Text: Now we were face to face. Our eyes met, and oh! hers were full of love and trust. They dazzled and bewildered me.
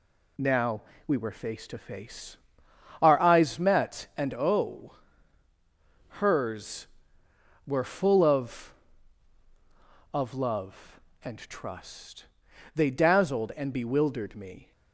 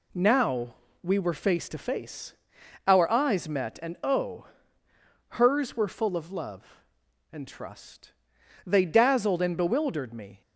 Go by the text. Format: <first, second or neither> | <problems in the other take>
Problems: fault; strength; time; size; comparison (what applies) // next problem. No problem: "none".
second | pauses between "Now" and "we"; slight; at 0.8 s; 0.24 s long; slight in the second // says "of" twice; at 10.1 s